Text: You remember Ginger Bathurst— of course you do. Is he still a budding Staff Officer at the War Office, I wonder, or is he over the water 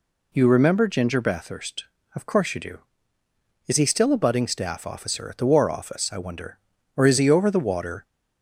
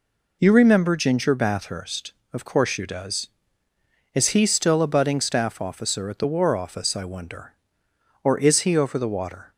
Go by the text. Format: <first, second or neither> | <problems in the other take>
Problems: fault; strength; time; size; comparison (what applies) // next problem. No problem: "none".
first | says "does" for "do"; at 2.8 s